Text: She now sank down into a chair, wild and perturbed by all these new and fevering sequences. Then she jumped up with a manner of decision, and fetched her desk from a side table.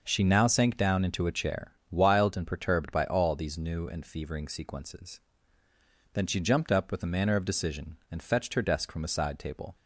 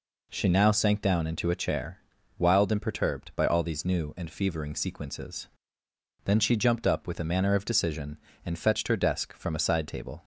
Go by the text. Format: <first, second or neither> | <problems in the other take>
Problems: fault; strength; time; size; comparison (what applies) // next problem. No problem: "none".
neither | none